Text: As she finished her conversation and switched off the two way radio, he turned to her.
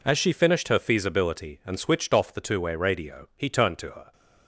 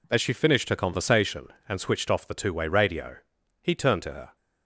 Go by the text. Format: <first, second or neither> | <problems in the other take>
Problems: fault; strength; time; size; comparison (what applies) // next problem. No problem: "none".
second | says "feasibility" for "conversation"; at 0.7 s